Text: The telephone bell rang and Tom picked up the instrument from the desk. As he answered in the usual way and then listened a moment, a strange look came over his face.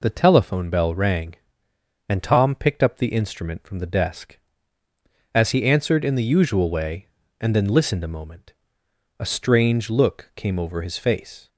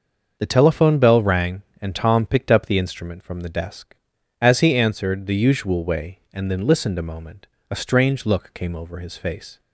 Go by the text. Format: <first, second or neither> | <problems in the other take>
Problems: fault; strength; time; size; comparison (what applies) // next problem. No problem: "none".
first | starts louder than the rest; until 1.4 s; 6.5 dB // skips "in"; at 5.2 s